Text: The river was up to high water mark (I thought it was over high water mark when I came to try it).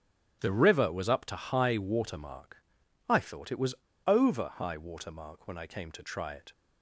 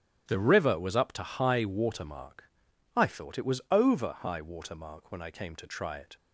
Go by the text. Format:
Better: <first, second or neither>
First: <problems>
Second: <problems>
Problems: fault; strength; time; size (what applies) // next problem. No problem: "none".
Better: second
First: starts louder than the rest; strong; until 1.4 s; 9.5 dB // pauses between "was" and "over"; slight; at 3.7 s; 0.30 s long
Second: starts louder than the rest; strong; until 1.2 s; 9.5 dB